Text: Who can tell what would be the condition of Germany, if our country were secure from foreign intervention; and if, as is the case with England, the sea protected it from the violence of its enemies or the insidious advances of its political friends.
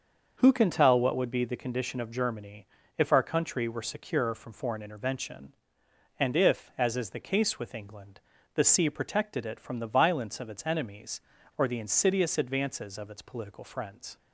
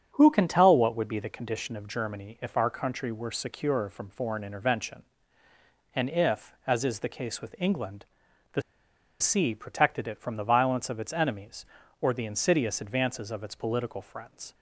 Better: first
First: starts louder than the rest; until 1.3 s; 6.5 dB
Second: starts louder than the rest; strong; until 1.1 s; 8 dB // pauses between "the" and "sea"; noticeable; at 8.5 s; 0.60 s long

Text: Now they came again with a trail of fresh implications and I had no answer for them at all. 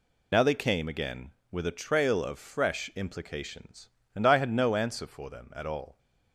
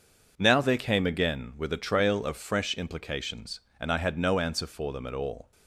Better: second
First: loses the start of "Now"; at 0.3 s; 30 ms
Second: none

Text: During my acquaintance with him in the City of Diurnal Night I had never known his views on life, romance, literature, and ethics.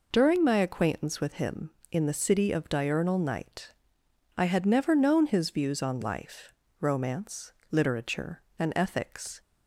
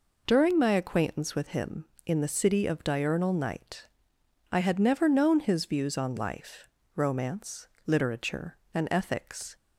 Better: neither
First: pauses between "Night" and "I"; noticeable; at 3.7 s; 0.64 s long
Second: pauses between "Night" and "I"; noticeable; at 3.8 s; 0.64 s long

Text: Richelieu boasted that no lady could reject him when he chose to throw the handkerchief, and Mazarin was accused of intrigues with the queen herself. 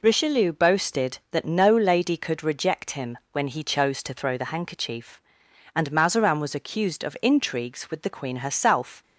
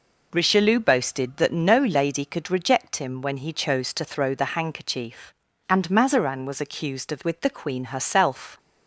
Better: first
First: none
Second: skips "intrigues"; at 7.2 s

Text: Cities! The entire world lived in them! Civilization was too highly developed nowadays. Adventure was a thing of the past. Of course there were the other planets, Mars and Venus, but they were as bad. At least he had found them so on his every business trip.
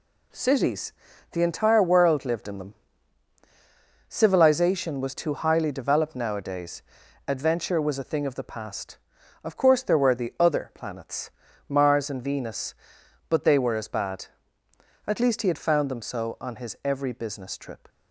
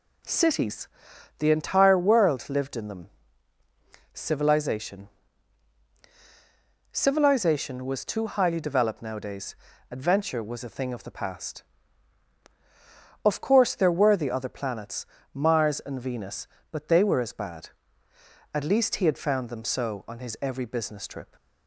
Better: first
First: none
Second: says "Civilization" twice; at 6.9 s

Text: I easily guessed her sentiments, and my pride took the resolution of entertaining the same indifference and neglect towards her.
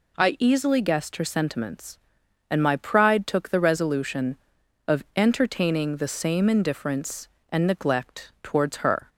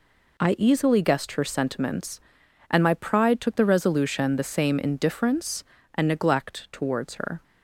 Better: first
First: none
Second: skips "of entertaining"; at 4.3 s

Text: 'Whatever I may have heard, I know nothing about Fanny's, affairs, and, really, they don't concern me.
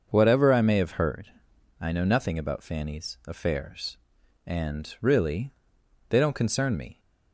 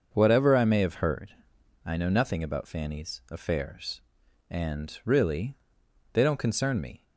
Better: neither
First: starts louder than the rest; until 1.1 s; 6 dB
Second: starts louder than the rest; until 1.1 s; 6 dB

